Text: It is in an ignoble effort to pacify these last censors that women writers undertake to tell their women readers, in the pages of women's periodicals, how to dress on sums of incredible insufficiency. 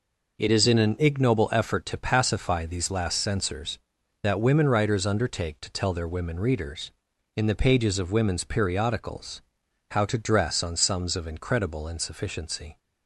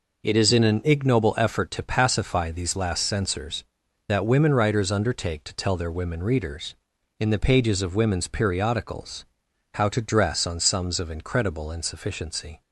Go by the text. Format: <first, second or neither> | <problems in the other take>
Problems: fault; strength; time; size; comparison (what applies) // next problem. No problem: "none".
neither | none